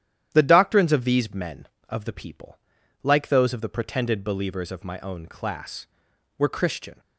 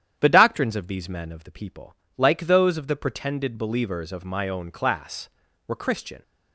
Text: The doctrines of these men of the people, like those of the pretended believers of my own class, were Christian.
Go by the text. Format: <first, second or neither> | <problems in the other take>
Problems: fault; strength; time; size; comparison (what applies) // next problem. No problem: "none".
neither | starts louder than the rest; strong; the same in both